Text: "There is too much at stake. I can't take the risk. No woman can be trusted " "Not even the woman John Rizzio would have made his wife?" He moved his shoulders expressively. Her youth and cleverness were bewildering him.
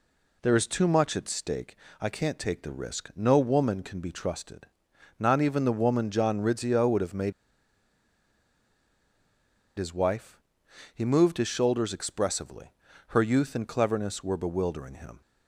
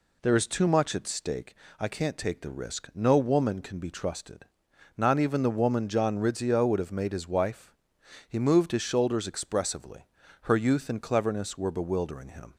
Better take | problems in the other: second | pauses between "made" and "his"; strong; at 7.3 s; 2.4 s long

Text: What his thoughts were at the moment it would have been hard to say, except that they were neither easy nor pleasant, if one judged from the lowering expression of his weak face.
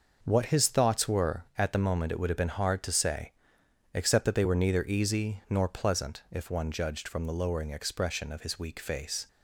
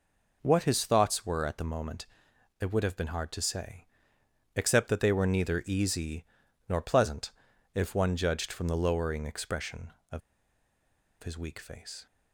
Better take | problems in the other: first | pauses between "moment" and "it"; noticeable; at 2.0 s; 0.56 s long // pauses between "easy" and "nor"; at 6.2 s; 0.44 s long // pauses between "of" and "his"; at 10.2 s; 1.0 s long

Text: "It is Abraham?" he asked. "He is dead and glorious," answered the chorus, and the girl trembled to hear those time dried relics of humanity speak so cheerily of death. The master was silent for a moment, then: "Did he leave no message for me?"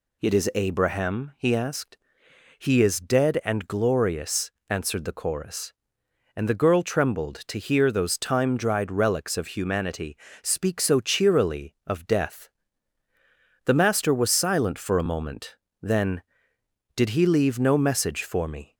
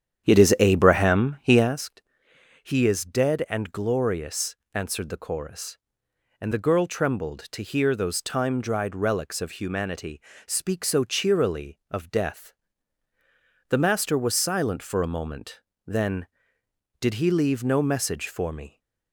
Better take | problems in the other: first | starts louder than the rest; strong; until 1.9 s; 9 dB // pauses between "humanity" and "speak"; slight; at 10.2 s; 0.26 s long; slight in the first

